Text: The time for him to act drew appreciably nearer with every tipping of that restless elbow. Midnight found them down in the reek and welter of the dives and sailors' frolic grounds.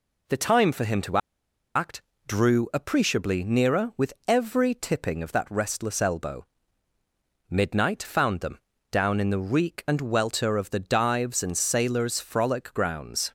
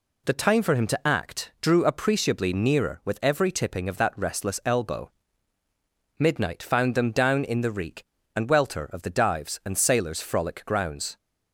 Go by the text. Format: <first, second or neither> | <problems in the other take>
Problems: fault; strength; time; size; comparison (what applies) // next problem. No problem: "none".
second | pauses between "to" and "act"; noticeable; at 1.1 s; 0.57 s long // pauses between "act" and "drew"; slight; at 2.0 s; 0.26 s long // pauses between "them" and "down"; slight; at 8.5 s; 0.34 s long